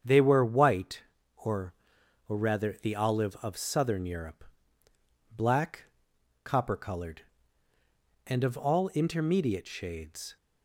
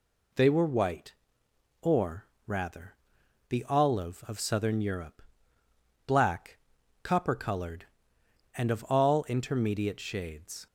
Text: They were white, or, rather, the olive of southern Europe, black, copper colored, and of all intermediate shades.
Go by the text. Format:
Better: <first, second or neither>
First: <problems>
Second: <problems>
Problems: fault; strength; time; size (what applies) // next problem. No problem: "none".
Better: second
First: starts louder than the rest; strong; until 1.3 s; 7.5 dB // says "or" twice; at 2.2 s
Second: none